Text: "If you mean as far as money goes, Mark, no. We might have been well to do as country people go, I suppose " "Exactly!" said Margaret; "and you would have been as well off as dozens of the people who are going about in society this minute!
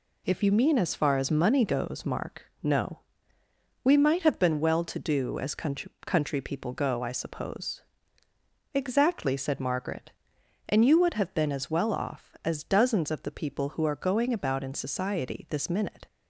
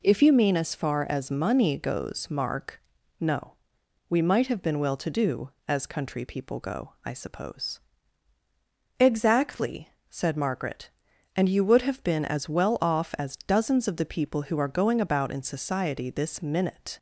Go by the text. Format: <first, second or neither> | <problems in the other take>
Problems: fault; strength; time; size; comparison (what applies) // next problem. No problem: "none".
second | says "country" twice; at 6.0 s